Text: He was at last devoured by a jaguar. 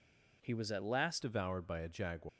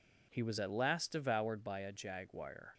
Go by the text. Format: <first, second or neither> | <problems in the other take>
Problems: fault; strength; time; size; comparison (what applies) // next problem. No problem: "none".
second | changes voice at "devoured"; from 1.2 s on; 1.0 s long